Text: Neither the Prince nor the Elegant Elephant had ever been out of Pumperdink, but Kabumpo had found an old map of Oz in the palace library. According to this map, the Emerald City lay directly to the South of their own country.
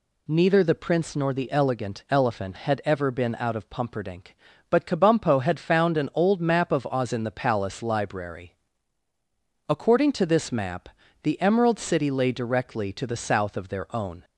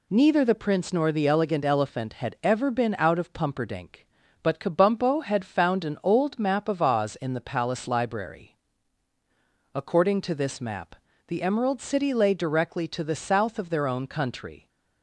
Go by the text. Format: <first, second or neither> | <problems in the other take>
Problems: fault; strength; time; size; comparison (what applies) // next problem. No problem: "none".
second | stops before "country"; at 14.2 s